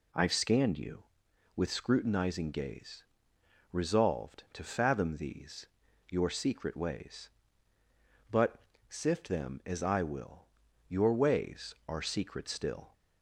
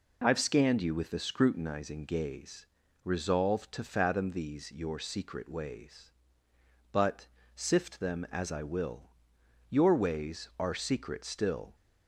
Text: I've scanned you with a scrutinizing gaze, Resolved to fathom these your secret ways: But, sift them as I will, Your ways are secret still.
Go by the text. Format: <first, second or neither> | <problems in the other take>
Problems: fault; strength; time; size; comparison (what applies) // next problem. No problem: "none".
second | skips "a"; at 1.7 s // pauses between "these" and "your"; at 5.6 s; 0.42 s long